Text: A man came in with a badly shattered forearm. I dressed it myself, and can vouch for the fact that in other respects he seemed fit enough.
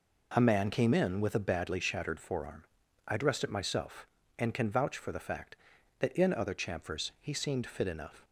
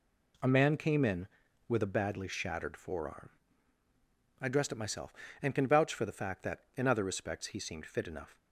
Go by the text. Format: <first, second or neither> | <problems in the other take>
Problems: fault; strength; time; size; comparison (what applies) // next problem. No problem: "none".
second | says "chamfers" for "respects"; at 6.5 s